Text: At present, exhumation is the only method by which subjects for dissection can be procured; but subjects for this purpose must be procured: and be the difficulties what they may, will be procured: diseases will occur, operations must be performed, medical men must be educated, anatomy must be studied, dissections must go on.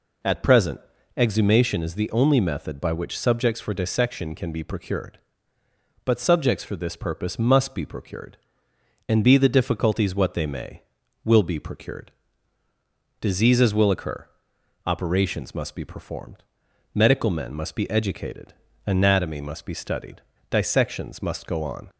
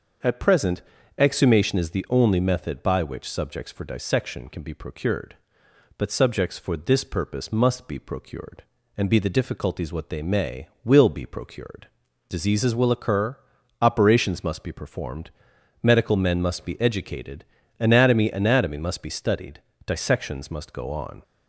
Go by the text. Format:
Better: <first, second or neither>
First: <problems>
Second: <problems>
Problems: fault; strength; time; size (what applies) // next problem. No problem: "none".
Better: first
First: none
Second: starts louder than the rest; until 1.5 s; 6.5 dB // says "anatomy" twice; at 18.3 s